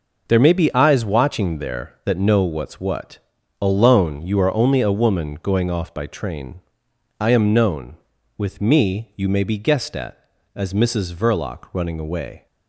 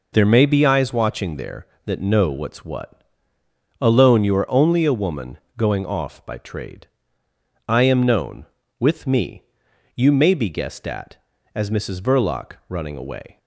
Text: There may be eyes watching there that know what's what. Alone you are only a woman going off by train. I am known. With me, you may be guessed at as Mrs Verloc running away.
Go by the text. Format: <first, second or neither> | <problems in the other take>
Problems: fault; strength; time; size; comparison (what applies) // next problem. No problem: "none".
first | pauses between "woman" and "going"; slight; at 5.3 s; 0.20 s long // says "trade" for "train"; at 6.3 s // pauses between "Verloc" and "running"; slight; at 12.5 s; 0.18 s long